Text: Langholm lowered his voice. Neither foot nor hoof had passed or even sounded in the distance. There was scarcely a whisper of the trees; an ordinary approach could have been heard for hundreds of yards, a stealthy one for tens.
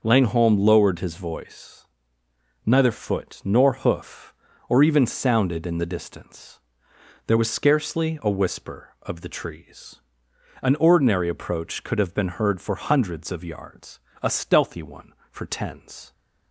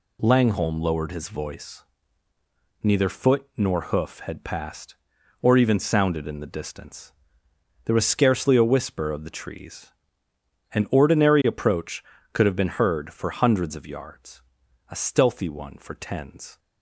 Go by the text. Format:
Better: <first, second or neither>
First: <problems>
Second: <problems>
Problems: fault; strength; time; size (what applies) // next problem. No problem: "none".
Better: second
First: skips "had passed"; at 4.5 s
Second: none